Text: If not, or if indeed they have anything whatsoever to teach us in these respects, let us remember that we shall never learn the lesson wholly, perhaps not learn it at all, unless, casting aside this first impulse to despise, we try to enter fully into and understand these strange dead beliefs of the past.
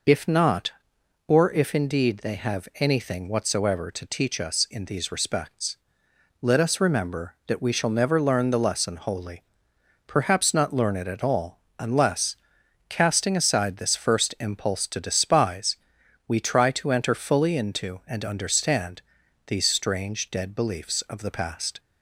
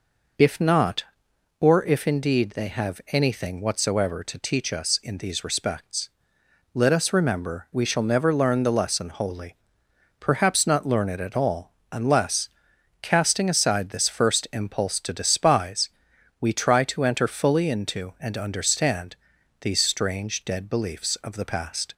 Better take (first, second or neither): first